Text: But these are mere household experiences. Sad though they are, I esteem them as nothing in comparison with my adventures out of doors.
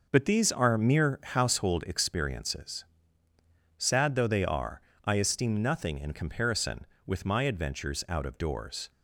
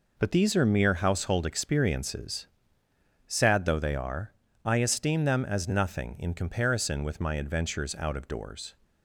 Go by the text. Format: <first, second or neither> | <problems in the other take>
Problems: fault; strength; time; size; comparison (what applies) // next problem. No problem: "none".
second | skips "them as"; at 5.6 s